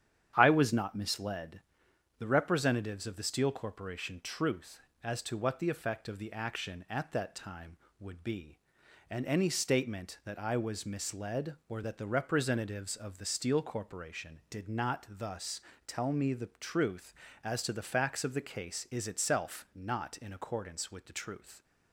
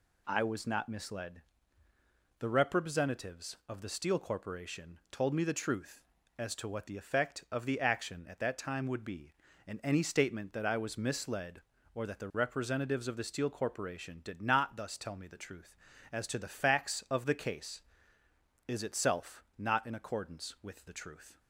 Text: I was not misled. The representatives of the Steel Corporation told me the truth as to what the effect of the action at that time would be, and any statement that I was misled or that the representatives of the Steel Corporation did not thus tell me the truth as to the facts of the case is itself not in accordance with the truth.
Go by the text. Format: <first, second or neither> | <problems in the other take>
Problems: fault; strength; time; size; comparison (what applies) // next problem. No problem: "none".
second | starts louder than the rest; strong; until 1.3 s; 9.5 dB // skips "told me the"; at 4.2 s // pauses between "thus" and "tell"; slight; at 15.5 s; 0.26 s long